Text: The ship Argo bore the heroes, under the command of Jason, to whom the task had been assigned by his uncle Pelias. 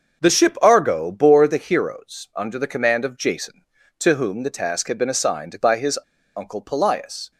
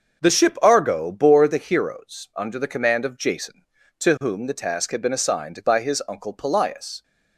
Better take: second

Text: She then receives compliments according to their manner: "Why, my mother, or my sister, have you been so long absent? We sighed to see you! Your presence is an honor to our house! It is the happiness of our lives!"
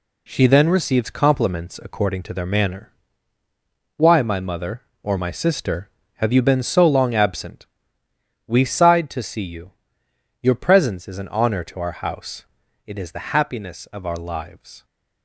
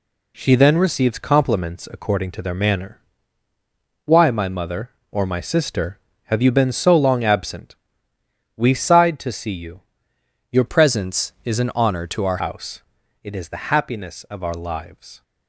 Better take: first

